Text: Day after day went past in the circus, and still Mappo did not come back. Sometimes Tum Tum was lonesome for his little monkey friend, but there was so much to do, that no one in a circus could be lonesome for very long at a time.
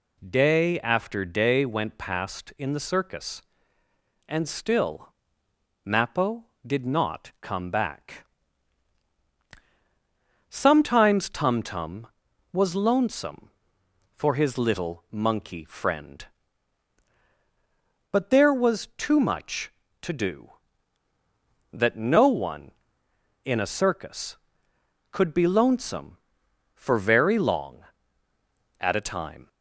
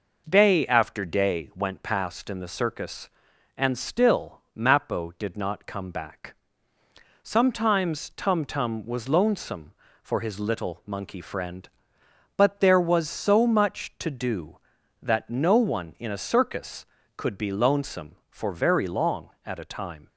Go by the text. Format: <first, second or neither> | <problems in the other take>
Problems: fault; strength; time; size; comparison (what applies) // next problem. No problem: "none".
second | pauses between "still" and "Mappo"; noticeable; at 5.0 s; 0.76 s long; slight in the second // says "too" for "so"; at 18.9 s